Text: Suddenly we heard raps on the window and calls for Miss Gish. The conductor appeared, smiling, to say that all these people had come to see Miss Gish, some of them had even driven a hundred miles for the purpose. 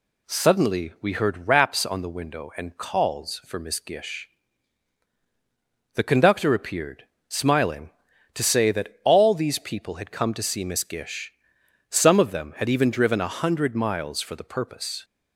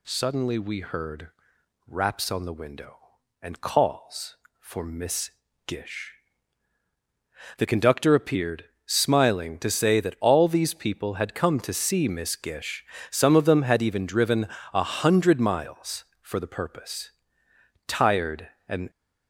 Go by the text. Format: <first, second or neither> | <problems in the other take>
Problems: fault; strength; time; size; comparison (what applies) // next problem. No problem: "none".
first | pauses between "heard" and "raps"; noticeable; at 1.2 s; 0.58 s long // pauses between "Miss" and "Gish"; slight; at 5.3 s; 0.34 s long // pauses between "driven" and "a"; slight; at 14.4 s; 0.26 s long // goes on to say "Tired and"; noticeable; from 17.8 s on; 1.0 s long